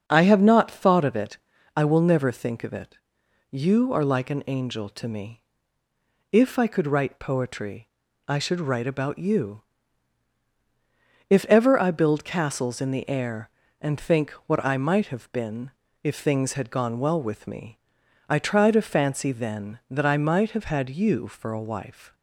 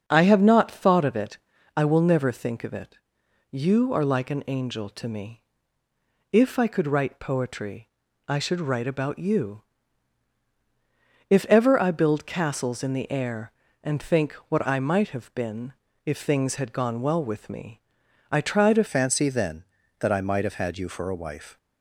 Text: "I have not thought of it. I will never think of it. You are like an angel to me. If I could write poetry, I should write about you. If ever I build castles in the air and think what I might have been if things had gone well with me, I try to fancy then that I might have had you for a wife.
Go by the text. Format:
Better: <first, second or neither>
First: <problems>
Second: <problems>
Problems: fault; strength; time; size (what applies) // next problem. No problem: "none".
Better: first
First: starts louder than the rest; until 1.0 s; 6.5 dB // pauses between "think" and "what"; slight; at 14.3 s; 0.16 s long // pauses between "been" and "if"; slight; at 15.7 s; 0.32 s long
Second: starts louder than the rest; until 1.0 s; 6.5 dB // pauses between "think" and "what"; slight; at 14.3 s; 0.16 s long // pauses between "been" and "if"; slight; at 15.7 s; 0.32 s long // changes voice at "fancy"; from 18.8 s on; 2.7 s long